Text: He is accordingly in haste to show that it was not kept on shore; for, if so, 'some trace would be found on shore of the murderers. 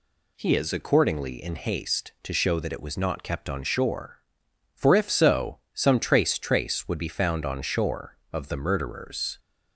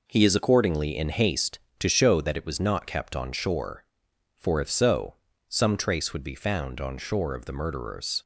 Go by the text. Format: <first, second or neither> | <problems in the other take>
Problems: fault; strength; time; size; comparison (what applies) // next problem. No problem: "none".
second | says "trace" twice; at 6.3 s